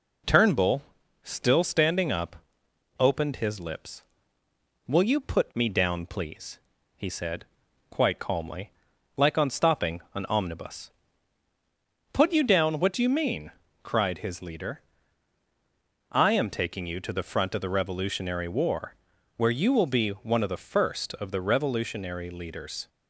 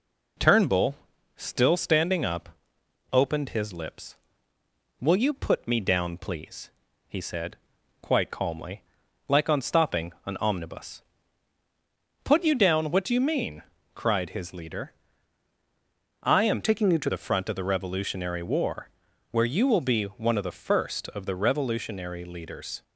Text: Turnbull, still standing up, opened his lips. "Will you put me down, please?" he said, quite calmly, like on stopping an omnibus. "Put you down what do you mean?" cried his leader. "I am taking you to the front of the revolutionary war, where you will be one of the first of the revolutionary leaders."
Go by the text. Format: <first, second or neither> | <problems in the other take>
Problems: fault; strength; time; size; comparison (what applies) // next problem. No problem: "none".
first | changes voice from "taking" to "to"; from 16.6 to 17.1 s; 0.5 s long